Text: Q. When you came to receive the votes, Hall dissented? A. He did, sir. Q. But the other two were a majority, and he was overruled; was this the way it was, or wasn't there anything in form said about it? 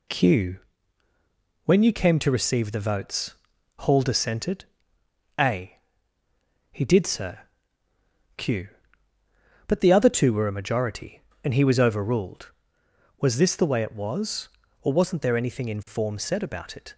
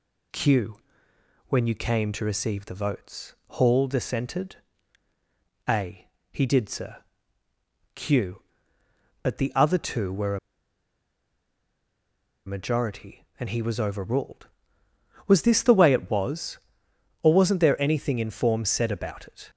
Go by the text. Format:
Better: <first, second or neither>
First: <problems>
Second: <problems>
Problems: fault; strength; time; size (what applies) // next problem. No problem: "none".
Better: first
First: none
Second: pauses between "a" and "majority"; strong; at 10.3 s; 2.0 s long